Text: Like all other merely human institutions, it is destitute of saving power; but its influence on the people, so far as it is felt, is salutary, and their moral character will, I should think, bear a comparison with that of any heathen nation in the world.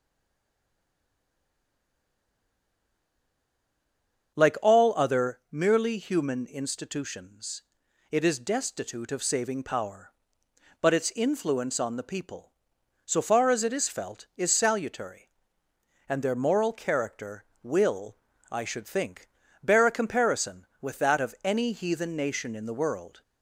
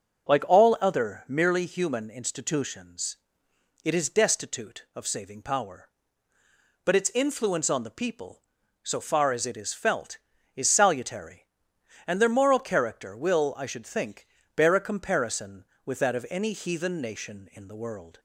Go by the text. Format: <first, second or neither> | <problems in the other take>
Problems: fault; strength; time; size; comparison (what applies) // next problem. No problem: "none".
second | stays silent before the first word; strong; until 4.3 s; 4.3 s long // starts louder than the rest; until 5.5 s; 6.5 dB